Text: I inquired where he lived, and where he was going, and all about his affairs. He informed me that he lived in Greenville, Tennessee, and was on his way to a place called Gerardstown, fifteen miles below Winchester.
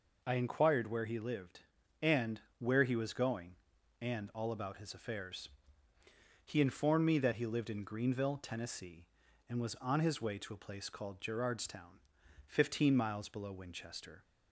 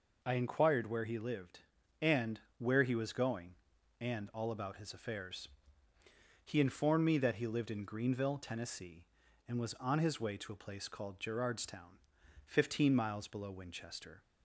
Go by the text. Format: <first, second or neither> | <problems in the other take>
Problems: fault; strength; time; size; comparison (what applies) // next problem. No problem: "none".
neither | pauses between "and" and "where"; slight; the same in both